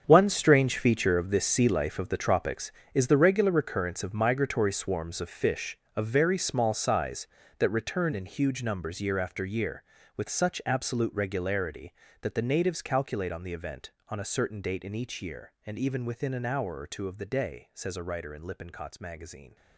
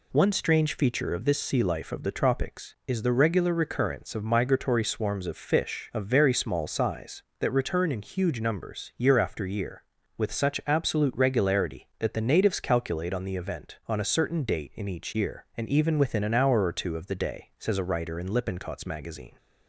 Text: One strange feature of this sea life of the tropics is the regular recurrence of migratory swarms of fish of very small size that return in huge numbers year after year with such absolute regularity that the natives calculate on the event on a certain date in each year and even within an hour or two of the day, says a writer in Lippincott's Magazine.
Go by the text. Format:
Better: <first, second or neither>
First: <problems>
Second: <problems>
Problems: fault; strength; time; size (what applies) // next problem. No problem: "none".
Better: second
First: gets quieter; strong; throughout; 13.5 dB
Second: none